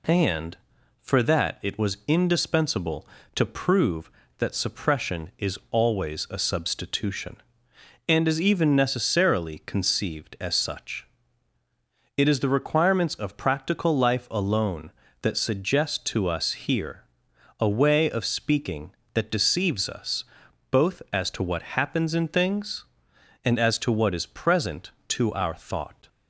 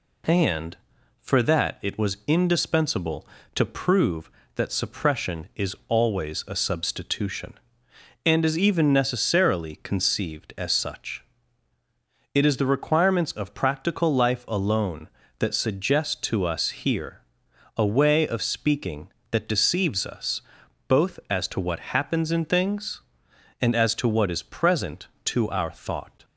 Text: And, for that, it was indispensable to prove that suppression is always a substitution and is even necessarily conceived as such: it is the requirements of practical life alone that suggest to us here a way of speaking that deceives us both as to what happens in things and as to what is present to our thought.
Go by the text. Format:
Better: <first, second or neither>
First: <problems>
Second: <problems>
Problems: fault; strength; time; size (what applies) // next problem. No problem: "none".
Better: neither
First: pauses between "here" and "a"; noticeable; at 17.0 s; 0.56 s long // pauses between "us" and "both"; noticeable; at 20.2 s; 0.46 s long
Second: pauses between "here" and "a"; noticeable; at 17.2 s; 0.56 s long // pauses between "us" and "both"; noticeable; at 20.4 s; 0.46 s long